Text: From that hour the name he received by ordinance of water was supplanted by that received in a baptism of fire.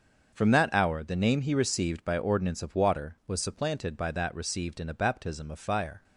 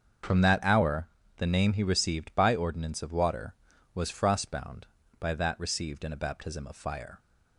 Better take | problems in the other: first | starts louder than the rest; until 1.5 s; 7 dB; also in the first // pauses between "hour" and "the"; slight; at 1.0 s; 0.30 s long // says "frostbound" for "supplanted"; at 4.1 s

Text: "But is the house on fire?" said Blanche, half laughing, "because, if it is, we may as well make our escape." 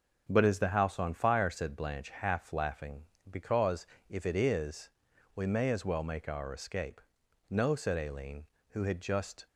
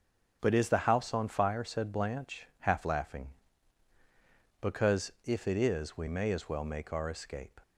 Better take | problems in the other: second | starts louder than the rest; until 1.3 s; 6.5 dB; also in the second // goes on to say "No said Aileen who had just"; strong; from 7.4 s on; 1.9 s long

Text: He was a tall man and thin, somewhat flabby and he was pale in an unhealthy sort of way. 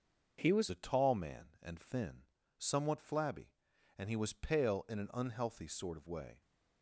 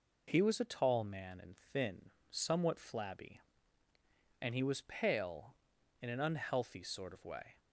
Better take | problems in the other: second | starts louder than the rest; noticeable; until 1.4 s; 6 dB // changes voice at "a"; from 0.7 s on; 5.7 s long

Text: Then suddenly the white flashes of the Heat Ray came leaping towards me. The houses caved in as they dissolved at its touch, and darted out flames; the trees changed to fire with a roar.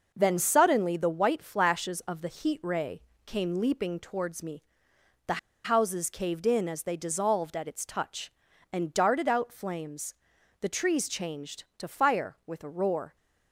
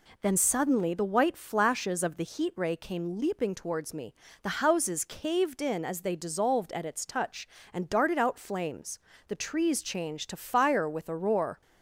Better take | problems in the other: second | pauses between "Ray" and "came"; slight; at 3.0 s; 0.24 s long // pauses between "The" and "houses"; slight; at 5.3 s; 0.25 s long

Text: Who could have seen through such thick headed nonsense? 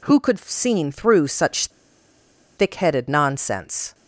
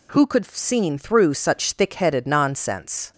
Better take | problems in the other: second | pauses between "such" and "thick"; noticeable; at 1.6 s; 0.89 s long

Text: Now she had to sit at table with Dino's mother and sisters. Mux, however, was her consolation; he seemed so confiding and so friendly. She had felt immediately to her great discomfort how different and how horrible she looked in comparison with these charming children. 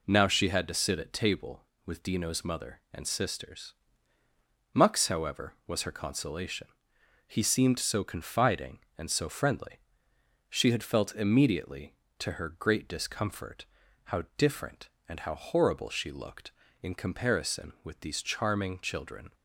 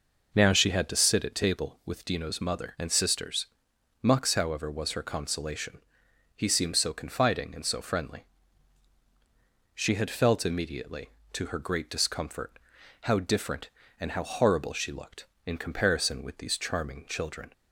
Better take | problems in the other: neither | pauses between "discomfort" and "how"; the same in both

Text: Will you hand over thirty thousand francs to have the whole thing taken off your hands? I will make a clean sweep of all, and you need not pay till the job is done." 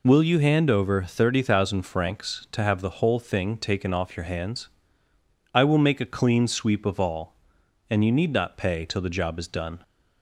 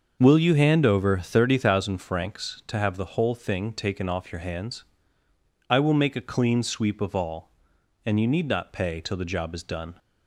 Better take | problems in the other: first | starts louder than the rest; until 1.9 s; 6.5 dB

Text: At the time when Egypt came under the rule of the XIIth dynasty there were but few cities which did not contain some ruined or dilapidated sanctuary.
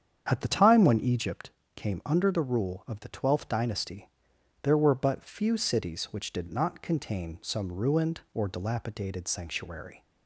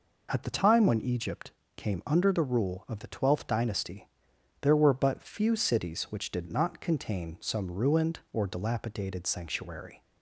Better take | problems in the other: second | starts louder than the rest; strong; until 1.4 s; 8 dB // pauses between "Egypt" and "came"; slight; at 1.5 s; 0.26 s long; slight in the second // pauses between "dynasty" and "there"; noticeable; at 4.0 s; 0.52 s long; noticeable in the second

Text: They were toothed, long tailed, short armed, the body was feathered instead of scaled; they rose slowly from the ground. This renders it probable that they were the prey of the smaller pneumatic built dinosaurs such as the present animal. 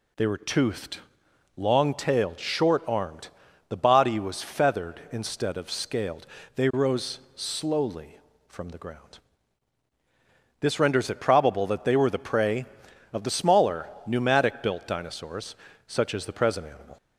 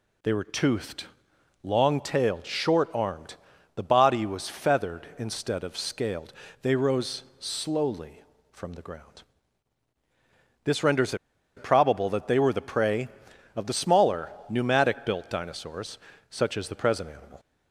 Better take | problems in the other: first | pauses between "rose" and "slowly"; slight; at 7.2 s; 0.16 s long; slight in the first // pauses between "renders" and "it"; at 11.1 s; 0.41 s long // pauses between "smaller" and "pneumatic"; slight; at 14.3 s; 0.18 s long; slight in the first // pauses between "dinosaurs" and "such"; slight; at 15.9 s; 0.32 s long; slight in the first

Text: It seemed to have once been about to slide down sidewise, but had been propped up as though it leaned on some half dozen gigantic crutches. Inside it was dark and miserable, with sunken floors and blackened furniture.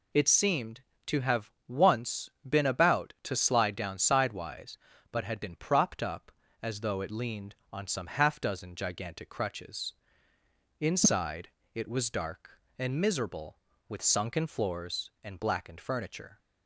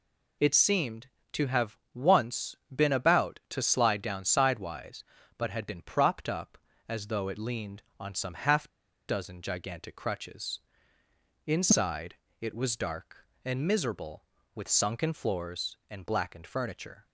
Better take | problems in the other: first | pauses between "once" and "been"; slight; at 2.5 s; 0.16 s long; slight in the first // pauses between "half" and "dozen"; at 8.6 s; 0.41 s long // pauses between "Inside" and "it"; slight; at 12.1 s; 0.26 s long; slight in the first

